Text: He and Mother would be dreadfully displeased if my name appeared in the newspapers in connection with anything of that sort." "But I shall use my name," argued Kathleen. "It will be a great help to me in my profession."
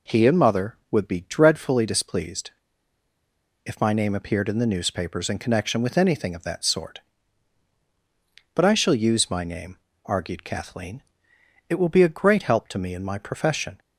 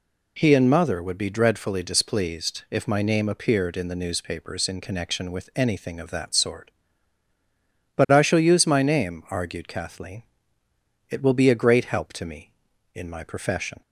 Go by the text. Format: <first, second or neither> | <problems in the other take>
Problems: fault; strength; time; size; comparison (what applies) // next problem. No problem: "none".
second | pauses between "displeased" and "if"; at 2.5 s; 1.1 s long